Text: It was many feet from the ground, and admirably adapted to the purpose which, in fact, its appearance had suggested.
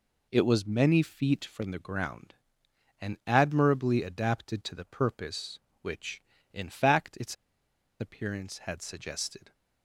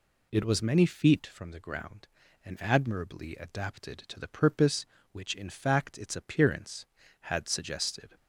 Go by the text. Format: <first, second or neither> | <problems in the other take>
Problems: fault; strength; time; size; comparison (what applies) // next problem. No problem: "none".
second | pauses between "its" and "appearance"; noticeable; at 7.3 s; 0.66 s long